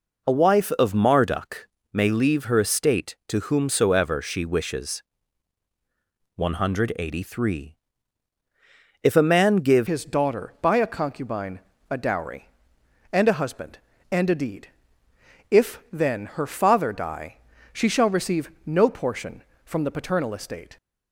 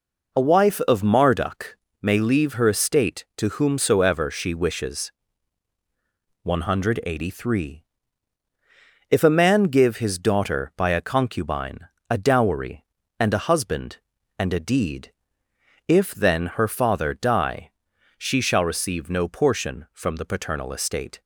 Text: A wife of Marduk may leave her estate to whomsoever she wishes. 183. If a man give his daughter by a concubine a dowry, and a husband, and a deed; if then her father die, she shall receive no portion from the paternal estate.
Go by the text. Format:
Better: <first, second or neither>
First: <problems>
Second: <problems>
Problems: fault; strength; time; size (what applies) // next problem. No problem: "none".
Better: second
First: pauses between "Marduk" and "may"; slight; at 1.6 s; 0.24 s long // changes voice at "his"; from 9.8 s on; 10.9 s long // pauses between "concubine" and "a"; slight; at 11.6 s; 0.28 s long // pauses between "receive" and "no"; slight; at 18.5 s; 0.16 s long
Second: pauses between "Marduk" and "may"; slight; at 1.7 s; 0.24 s long // pauses between "concubine" and "a"; slight; at 11.8 s; 0.20 s long